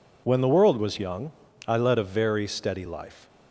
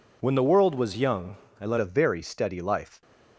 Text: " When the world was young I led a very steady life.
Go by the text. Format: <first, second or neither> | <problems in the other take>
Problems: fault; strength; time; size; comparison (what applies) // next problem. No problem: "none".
first | pauses between "young" and "I"; slight; at 1.3 s; 0.24 s long; slight in the first // changes voice at "a"; from 1.7 s on; 1.3 s long